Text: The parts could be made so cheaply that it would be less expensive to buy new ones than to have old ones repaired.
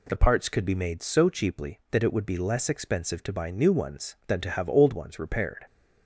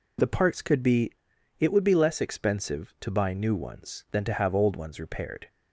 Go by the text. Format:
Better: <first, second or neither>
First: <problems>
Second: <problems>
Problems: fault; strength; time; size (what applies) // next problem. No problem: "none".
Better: first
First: none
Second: skips "made so cheaply that"; at 1.3 s